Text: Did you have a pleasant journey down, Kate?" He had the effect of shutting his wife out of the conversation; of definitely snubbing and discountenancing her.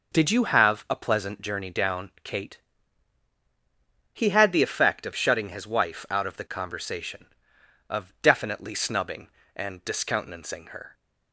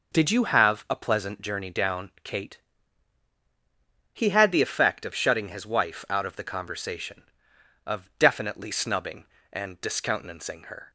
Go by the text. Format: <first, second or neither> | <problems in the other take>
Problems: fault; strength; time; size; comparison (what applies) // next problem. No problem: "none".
neither | none